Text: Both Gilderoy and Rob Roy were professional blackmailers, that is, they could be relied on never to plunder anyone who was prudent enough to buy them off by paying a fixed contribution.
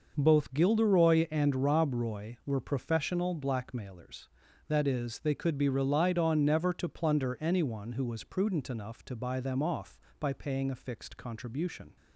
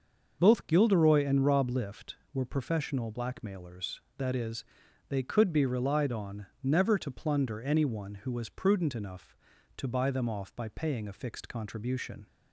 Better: first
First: none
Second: starts louder than the rest; until 1.4 s; 6.5 dB // says "Lift" for "Roy"; at 1.6 s // pauses between "on" and "never"; slight; at 6.4 s; 0.16 s long

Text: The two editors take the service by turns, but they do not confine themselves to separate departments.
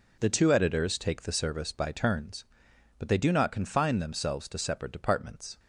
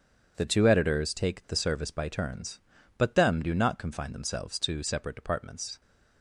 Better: first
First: none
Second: starts louder than the rest; strong; until 1.3 s; 7 dB // says "them" for "they"; at 3.1 s

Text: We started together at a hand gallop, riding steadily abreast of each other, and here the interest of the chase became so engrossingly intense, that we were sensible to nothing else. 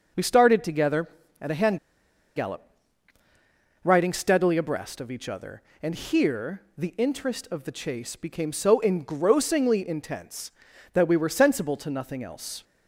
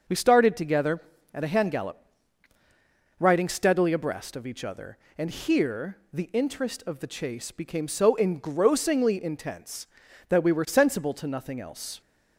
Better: second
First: pauses between "hand" and "gallop"; noticeable; at 1.7 s; 0.58 s long // pauses between "here" and "the"; slight; at 6.6 s; 0.16 s long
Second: pauses between "here" and "the"; slight; at 5.9 s; 0.16 s long

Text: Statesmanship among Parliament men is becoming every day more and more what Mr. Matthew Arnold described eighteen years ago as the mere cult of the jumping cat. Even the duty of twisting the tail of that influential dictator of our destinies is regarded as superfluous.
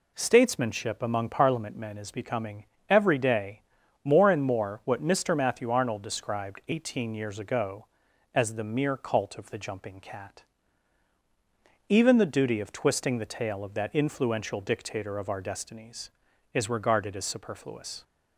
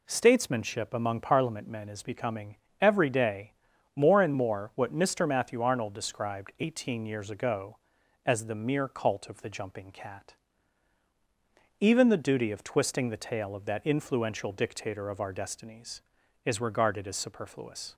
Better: neither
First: pauses between "becoming" and "every"; slight; at 2.6 s; 0.22 s long // pauses between "day" and "more"; at 3.6 s; 0.42 s long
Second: pauses between "becoming" and "every"; slight; at 2.5 s; 0.22 s long // pauses between "day" and "more"; at 3.5 s; 0.42 s long

